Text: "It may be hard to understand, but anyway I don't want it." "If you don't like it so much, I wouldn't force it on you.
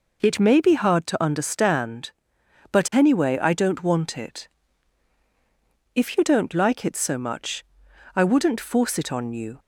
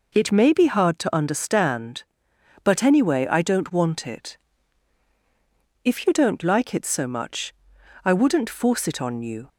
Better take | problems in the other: neither | none

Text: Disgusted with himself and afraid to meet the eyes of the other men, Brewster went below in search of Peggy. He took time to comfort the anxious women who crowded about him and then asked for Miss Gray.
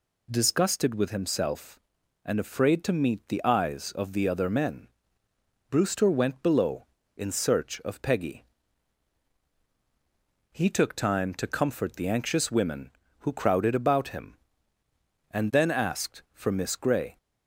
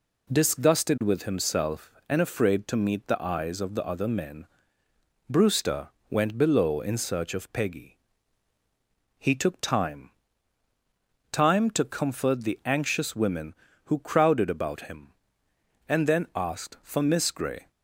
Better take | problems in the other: first | pauses between "Brewster" and "went"; slight; at 5.8 s; 0.20 s long // says "time" twice; at 11.3 s

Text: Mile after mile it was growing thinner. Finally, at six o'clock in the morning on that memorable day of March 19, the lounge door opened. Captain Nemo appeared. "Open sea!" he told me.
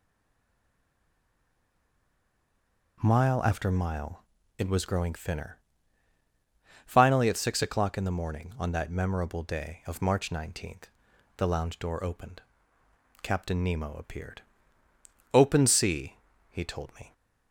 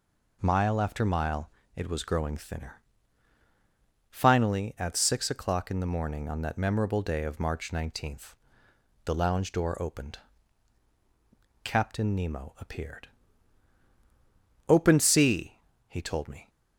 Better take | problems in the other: second | stays silent before the first word; strong; until 2.9 s; 2.9 s long // pauses between "mile" and "it"; slight; at 4.2 s; 0.34 s long; slight in the second

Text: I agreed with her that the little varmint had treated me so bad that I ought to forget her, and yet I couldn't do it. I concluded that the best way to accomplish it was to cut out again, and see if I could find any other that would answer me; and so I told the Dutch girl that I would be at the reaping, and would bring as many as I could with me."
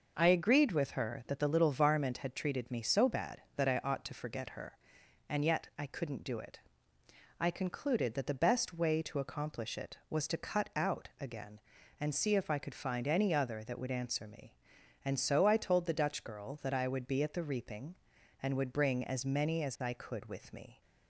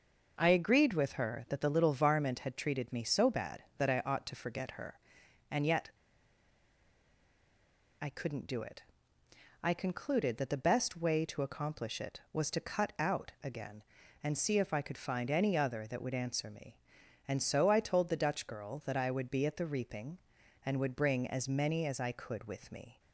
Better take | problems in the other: first | pauses between "yet" and "I"; strong; at 5.8 s; 2.1 s long

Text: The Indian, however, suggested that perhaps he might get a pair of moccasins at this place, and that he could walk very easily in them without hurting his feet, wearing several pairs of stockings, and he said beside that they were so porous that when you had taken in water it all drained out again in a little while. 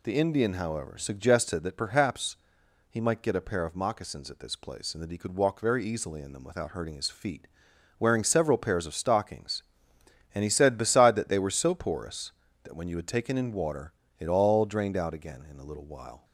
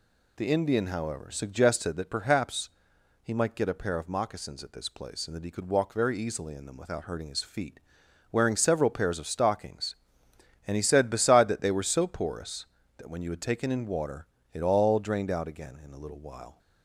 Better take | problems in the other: neither | pauses between "perhaps" and "he"; noticeable; the same in both // pauses between "water" and "it"; slight; the same in both

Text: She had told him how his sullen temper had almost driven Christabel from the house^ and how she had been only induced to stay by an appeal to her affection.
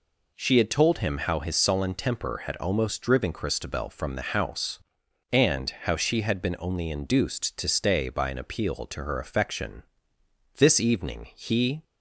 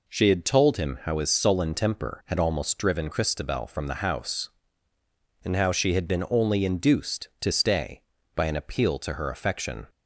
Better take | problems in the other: second | goes on to say "This evening he"; noticeable; from 10.5 s on; 1.2 s long

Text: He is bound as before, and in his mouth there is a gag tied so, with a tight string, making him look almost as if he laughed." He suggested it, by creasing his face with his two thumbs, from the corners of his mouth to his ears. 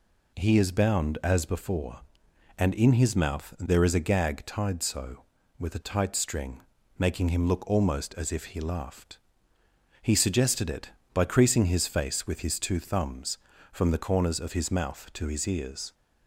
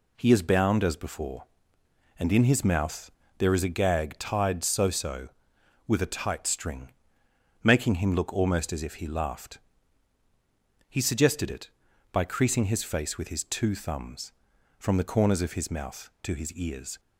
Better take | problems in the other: first | pauses between "mouth" and "there"; slight; at 3.1 s; 0.26 s long // says "so" twice; at 4.8 s

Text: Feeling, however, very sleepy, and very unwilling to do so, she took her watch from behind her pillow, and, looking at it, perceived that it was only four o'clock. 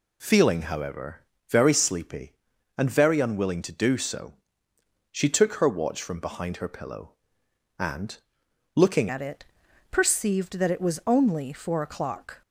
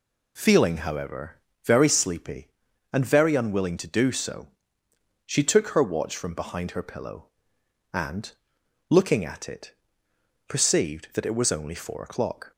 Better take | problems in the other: second | changes voice at "at"; from 9.0 s on; 3.4 s long

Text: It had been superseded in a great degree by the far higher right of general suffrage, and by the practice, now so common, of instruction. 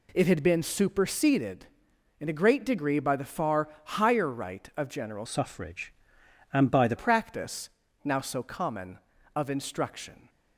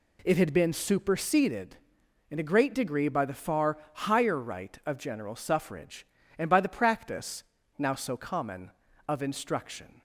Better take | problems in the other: second | pauses between "far" and "higher"; slight; at 3.6 s; 0.16 s long; slight in the second // changes voice from "suffrage" to "the"; from 5.2 to 6.9 s; 1.7 s long

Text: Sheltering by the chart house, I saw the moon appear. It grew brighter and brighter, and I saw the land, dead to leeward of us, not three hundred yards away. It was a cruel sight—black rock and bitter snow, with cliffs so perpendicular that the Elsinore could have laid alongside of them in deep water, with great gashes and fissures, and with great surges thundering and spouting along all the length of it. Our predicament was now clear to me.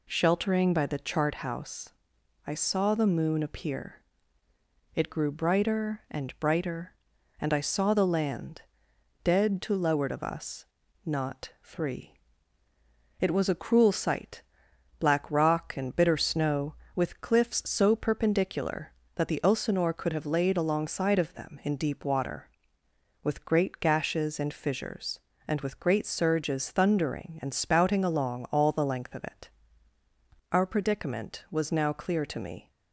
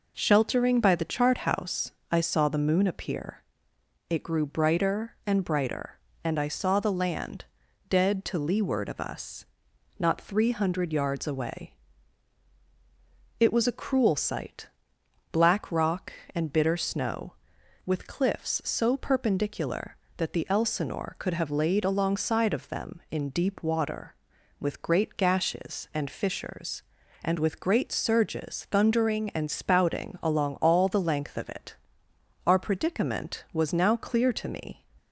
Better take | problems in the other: second | skips "hundred yards away"; at 12.6 s

